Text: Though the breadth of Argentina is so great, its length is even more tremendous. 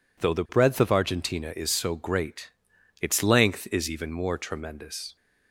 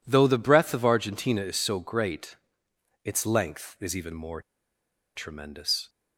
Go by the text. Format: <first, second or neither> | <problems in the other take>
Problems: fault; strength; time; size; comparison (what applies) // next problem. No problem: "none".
first | pauses between "more" and "tremendous"; noticeable; at 4.4 s; 0.75 s long